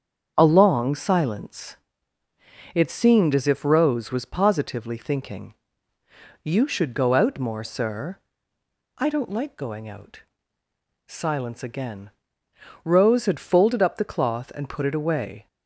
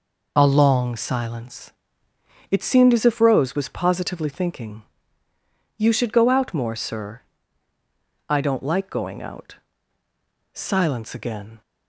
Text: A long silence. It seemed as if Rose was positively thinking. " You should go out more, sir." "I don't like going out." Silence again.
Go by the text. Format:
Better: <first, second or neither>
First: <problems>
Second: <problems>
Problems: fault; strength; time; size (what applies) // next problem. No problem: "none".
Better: second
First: starts louder than the rest; strong; until 1.3 s; 7.5 dB // goes on to say "Rose had folded up the cloth and put it away"; strong; from 12.8 s on; 2.6 s long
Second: none